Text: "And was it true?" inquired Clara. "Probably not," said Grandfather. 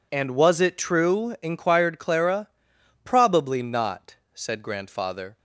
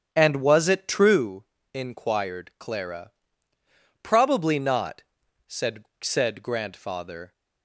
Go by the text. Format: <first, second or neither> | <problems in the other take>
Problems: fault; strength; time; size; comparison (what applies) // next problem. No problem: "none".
first | starts louder than the rest; strong; until 1.1 s; 8 dB // says "said" twice; at 6.0 s